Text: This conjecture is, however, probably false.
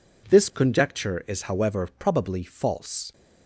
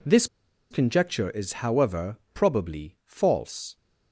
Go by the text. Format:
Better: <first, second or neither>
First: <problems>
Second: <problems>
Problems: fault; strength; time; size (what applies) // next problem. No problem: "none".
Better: first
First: none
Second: pauses between "This" and "conjecture"; at 0.2 s; 0.45 s long